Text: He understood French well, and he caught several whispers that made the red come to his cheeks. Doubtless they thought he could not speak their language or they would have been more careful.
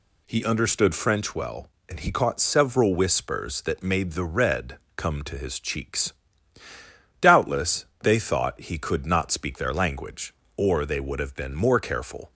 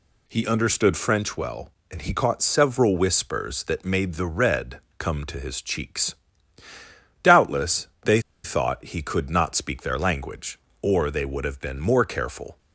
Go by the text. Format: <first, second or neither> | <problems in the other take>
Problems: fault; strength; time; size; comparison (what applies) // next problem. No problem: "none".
first | pauses between "red" and "come"; slight; at 4.7 s; 0.18 s long; slight in the first // pauses between "Doubtless" and "they"; slight; at 7.8 s; 0.16 s long; slight in the first // pauses between "they" and "thought"; slight; at 8.1 s; 0.24 s long